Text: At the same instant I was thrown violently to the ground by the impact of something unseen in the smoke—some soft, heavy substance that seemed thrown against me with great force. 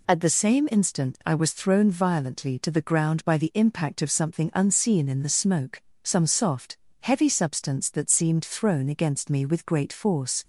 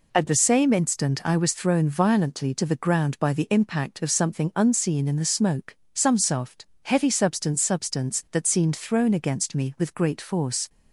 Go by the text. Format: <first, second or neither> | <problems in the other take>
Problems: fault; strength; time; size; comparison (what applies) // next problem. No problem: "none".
first | says "substance" twice; at 7.6 s